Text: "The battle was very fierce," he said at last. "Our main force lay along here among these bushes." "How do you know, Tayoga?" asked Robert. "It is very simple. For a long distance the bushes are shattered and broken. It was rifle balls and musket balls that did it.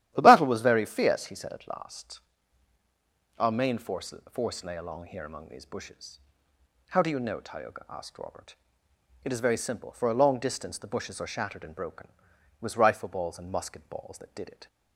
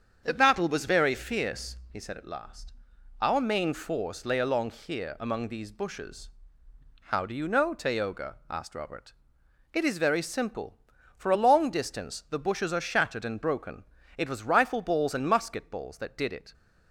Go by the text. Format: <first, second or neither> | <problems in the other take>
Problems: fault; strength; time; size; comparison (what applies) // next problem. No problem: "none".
second | starts louder than the rest; strong; until 1.1 s; 12.5 dB; strong in the second // says "force" twice; at 4.3 s